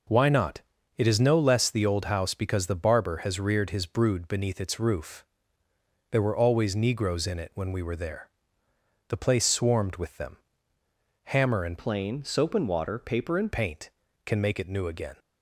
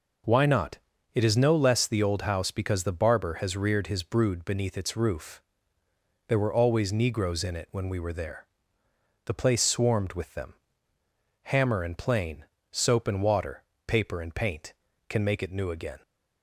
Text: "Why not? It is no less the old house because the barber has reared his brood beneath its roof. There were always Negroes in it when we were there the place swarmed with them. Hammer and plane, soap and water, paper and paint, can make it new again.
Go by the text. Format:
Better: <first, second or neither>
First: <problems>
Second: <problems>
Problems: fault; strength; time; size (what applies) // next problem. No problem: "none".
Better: second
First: pauses between "there" and "the"; noticeable; at 8.2 s; 0.82 s long // changes voice from "plane" to "and"; from 11.7 to 13.5 s; 1.8 s long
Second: pauses between "there" and "the"; noticeable; at 8.4 s; 0.82 s long